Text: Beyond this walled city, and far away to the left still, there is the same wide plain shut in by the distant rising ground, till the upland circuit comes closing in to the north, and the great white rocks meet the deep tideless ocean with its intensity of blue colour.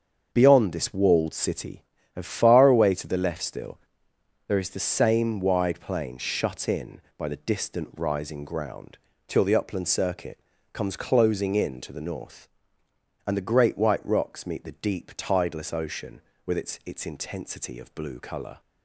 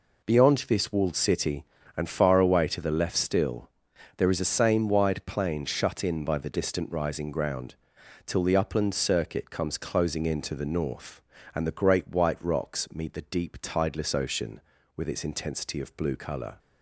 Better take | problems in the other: second | starts louder than the rest; until 1.3 s; 7 dB // pauses between "circuit" and "comes"; slight; at 10.3 s; 0.32 s long // says "its" twice; at 16.8 s

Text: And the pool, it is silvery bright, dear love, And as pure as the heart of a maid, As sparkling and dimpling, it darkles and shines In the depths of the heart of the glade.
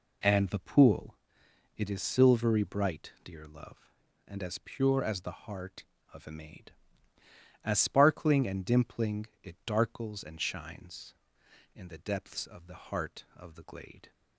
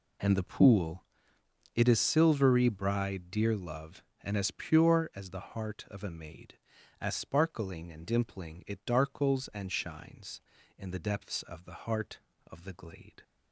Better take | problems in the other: first | says "bride" for "bright"; at 2.6 s

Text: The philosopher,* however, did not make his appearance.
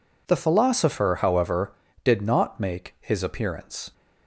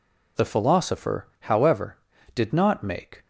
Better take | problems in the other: first | stops before "his appearance"; at 3.2 s

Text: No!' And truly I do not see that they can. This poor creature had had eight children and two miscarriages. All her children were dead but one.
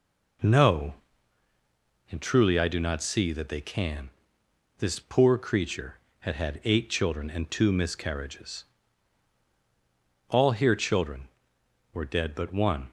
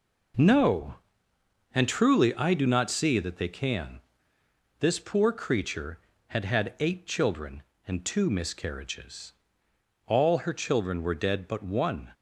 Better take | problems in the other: second | says "here" for "her"; at 10.5 s

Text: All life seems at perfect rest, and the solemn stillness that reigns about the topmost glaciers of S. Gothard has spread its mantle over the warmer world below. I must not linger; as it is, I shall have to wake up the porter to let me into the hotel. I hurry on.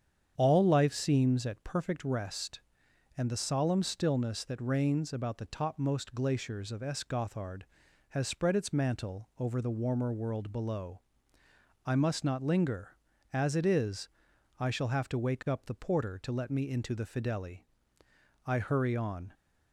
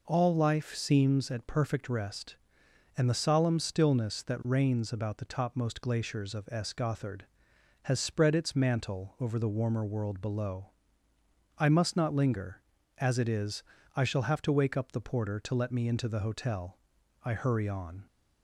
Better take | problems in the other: second | starts louder than the rest; strong; until 1.3 s; 8.5 dB // says "fideli" for "hotel"; at 17.0 s

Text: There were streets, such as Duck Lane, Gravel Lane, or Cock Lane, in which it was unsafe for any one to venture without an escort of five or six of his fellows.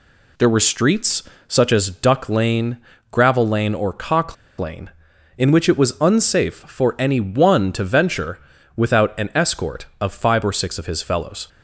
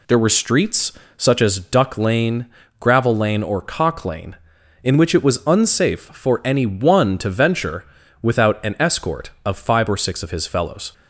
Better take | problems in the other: second | pauses between "Cock" and "Lane"; slight; at 4.3 s; 0.22 s long // pauses between "venture" and "without"; at 8.3 s; 0.38 s long; also in the second

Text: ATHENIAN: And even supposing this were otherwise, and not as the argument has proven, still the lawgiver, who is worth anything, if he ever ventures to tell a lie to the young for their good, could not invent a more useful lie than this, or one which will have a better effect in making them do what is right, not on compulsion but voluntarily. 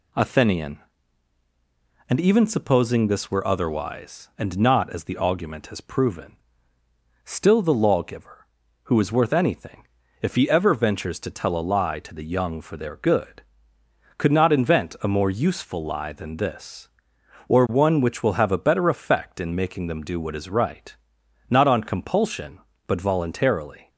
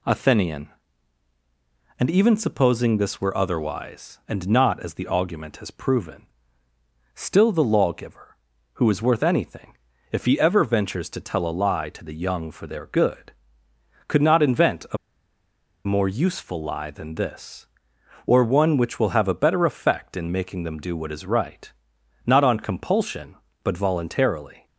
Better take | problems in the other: first | pauses between "a" and "more"; noticeable; at 14.9 s; 0.88 s long

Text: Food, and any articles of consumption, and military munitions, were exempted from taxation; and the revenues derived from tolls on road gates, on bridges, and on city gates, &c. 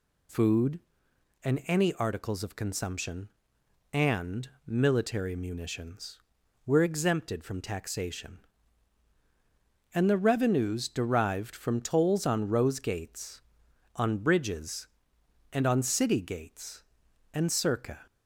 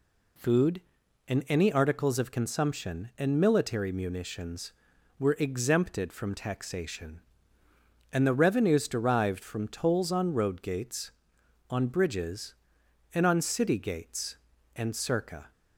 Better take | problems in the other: second | pauses between "and" and "military"; slight; at 4.4 s; 0.16 s long // says "rose" for "road"; at 12.4 s

